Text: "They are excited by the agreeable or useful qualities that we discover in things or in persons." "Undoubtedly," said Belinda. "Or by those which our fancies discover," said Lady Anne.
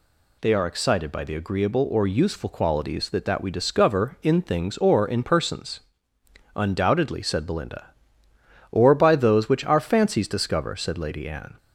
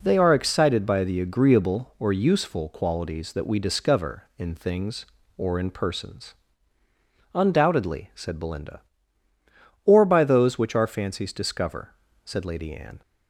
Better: second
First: says "that" twice; at 3.2 s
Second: none

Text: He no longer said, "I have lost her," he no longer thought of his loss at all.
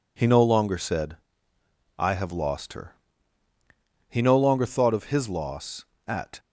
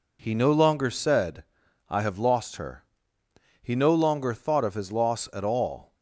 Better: second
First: stops before "all"; at 6.3 s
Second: none

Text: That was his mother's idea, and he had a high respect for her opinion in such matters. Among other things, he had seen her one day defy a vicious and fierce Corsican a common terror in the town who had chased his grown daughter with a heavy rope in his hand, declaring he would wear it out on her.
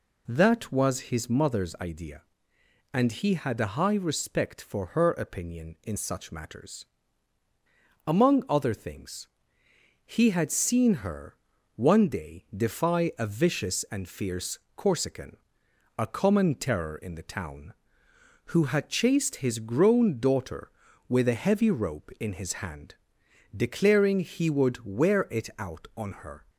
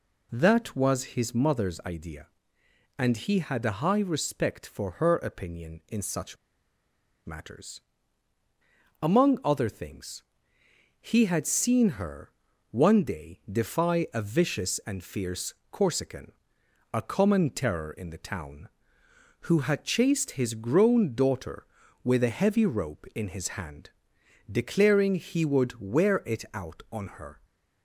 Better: first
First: pauses between "her" and "one"; at 11.3 s; 0.40 s long // pauses between "fierce" and "Corsican"; slight; at 14.5 s; 0.16 s long // pauses between "Corsican" and "a"; noticeable; at 15.3 s; 0.58 s long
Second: pauses between "such" and "matters"; noticeable; at 6.3 s; 0.90 s long // pauses between "her" and "one"; at 12.3 s; 0.40 s long // pauses between "fierce" and "Corsican"; slight; at 15.5 s; 0.16 s long // pauses between "Corsican" and "a"; noticeable; at 16.3 s; 0.58 s long

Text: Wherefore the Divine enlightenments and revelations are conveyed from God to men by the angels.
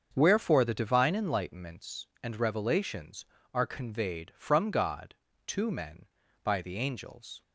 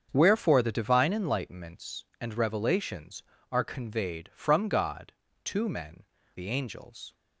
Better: first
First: starts louder than the rest; until 1.1 s; 7 dB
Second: starts louder than the rest; strong; until 1.1 s; 7.5 dB // skips "by"; at 6.1 s

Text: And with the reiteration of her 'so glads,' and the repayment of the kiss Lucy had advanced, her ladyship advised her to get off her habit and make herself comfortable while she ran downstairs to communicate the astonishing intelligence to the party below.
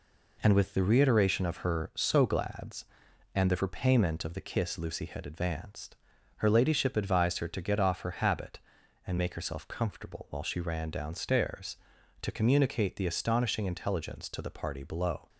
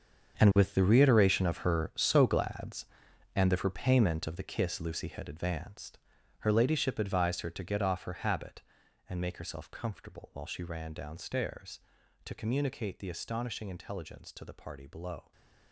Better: first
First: none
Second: gets quieter; strong; throughout; 14 dB // stays silent after the last word; slight; from 15.2 s on; 0.5 s long

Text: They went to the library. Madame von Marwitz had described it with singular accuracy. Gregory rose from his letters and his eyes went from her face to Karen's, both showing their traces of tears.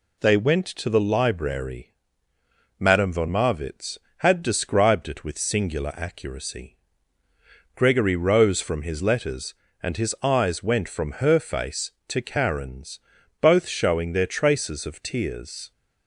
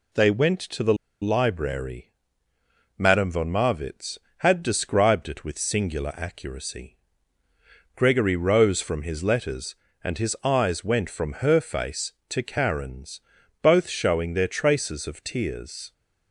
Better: first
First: none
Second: pauses between "the" and "library"; slight; at 0.9 s; 0.27 s long

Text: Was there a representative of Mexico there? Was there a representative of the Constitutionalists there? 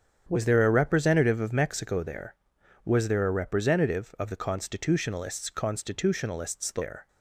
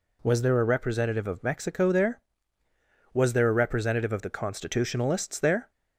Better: second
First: starts louder than the rest; strong; until 1.3 s; 8 dB // says "Constitutionalists" twice; at 5.4 s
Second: none

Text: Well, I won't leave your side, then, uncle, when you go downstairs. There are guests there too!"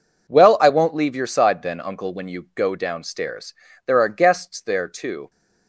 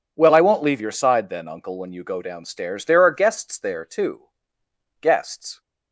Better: first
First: none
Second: goes on to say "Guests"; from 5.0 s on; 0.60 s long

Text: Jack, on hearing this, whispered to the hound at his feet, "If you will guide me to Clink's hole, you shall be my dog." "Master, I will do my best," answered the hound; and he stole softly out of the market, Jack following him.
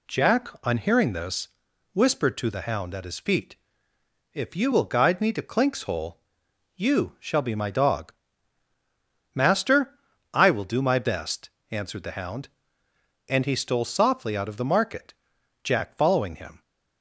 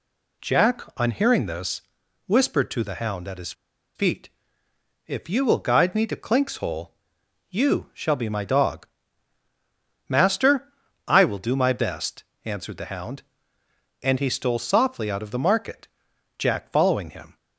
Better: first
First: none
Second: pauses between "his" and "feet"; at 3.5 s; 0.43 s long

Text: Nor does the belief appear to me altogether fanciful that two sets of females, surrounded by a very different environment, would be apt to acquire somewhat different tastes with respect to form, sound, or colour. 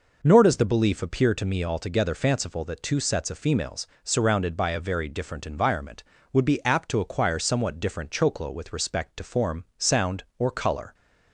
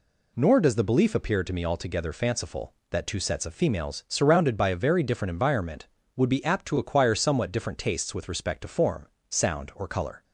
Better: second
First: says "choclo" for "tastes"; at 8.1 s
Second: none

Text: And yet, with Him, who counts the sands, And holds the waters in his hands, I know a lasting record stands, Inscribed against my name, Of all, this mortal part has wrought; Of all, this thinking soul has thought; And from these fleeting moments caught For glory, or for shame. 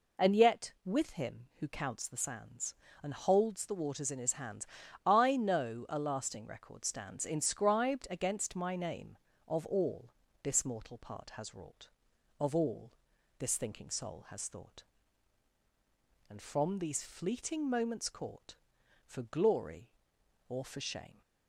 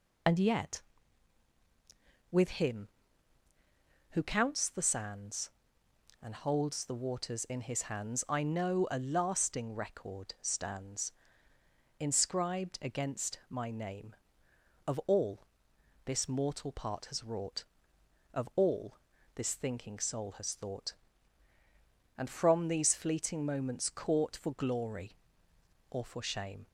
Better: first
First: none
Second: loses the start of "And"; at 0.2 s; 45 ms

